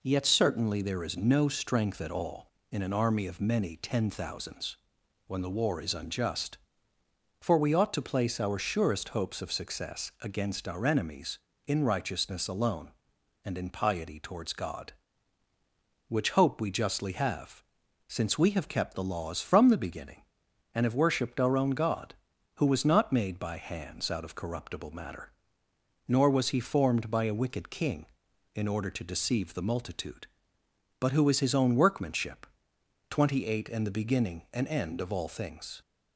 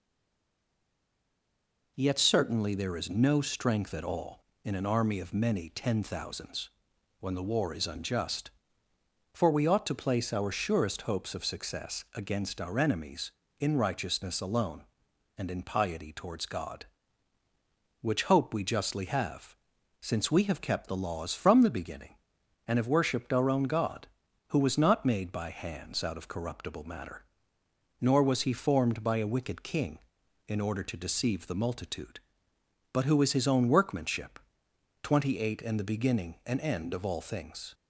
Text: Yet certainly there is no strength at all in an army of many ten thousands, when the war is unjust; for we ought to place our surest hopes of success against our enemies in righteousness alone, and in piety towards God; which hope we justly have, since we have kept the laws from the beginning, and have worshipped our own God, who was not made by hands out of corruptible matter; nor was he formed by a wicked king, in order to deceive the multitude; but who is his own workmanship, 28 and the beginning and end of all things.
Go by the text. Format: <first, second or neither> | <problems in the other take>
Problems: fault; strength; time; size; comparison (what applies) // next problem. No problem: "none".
first | stays silent before the first word; noticeable; until 1.9 s; 1.9 s long